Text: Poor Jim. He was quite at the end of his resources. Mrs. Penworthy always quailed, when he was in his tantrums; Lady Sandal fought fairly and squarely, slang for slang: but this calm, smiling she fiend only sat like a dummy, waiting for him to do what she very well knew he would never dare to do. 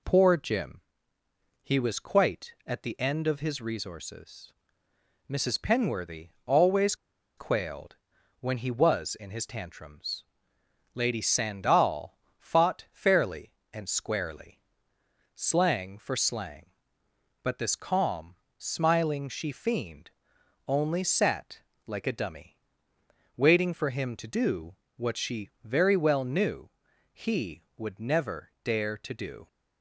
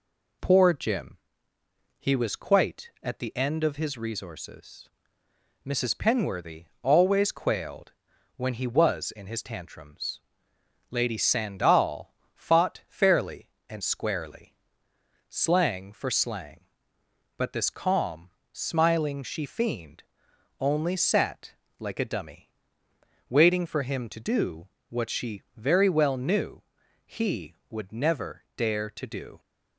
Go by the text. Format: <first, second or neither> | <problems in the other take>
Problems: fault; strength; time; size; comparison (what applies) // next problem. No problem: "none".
second | pauses between "always" and "quailed"; at 6.9 s; 0.42 s long // pauses between "Sandal" and "fought"; slight; at 12.1 s; 0.20 s long; slight in the second // pauses between "fiend" and "only"; noticeable; at 20.0 s; 0.58 s long; noticeable in the second // pauses between "sat" and "like"; slight; at 21.6 s; 0.26 s long; slight in the second // pauses between "do" and "what"; slight; at 24.7 s; 0.22 s long; slight in the second // pauses between "knew" and "he"; at 26.6 s; 0.44 s long; also in the second